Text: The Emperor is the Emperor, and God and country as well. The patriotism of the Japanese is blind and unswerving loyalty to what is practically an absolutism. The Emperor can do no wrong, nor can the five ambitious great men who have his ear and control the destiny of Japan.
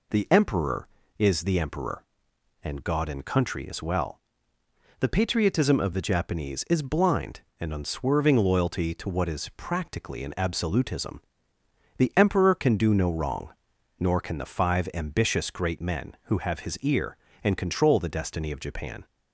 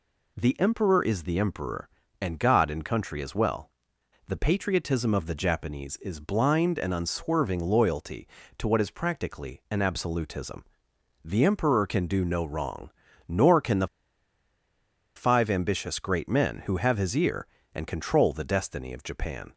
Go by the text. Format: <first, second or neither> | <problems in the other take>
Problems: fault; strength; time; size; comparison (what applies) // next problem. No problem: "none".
first | pauses between "the" and "five"; strong; at 13.8 s; 1.2 s long